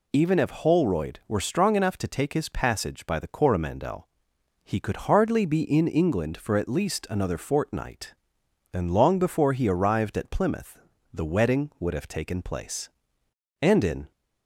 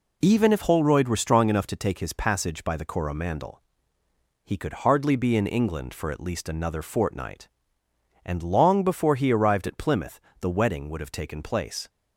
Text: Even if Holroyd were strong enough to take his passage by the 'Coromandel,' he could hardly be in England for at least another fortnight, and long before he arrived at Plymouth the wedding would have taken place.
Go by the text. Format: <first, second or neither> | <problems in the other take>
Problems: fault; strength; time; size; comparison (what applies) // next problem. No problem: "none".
second | pauses between "Plymouth" and "the"; slight; at 10.7 s; 0.36 s long; slight in the second // goes on to say "And in"; from 13.6 s on; 0.50 s long